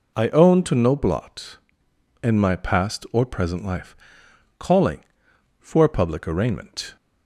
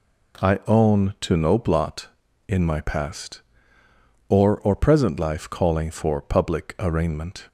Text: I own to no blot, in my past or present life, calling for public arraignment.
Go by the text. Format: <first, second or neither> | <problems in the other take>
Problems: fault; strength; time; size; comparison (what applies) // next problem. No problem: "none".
first | says "or" twice; at 4.5 s